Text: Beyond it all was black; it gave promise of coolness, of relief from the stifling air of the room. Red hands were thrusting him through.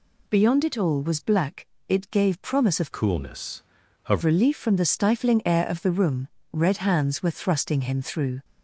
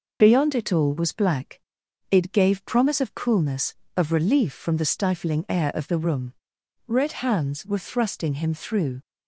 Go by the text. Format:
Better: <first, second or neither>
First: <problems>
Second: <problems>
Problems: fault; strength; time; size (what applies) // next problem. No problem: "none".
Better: second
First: changes voice from "coolness" to "of"; from 2.9 to 4.2 s; 1.3 s long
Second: none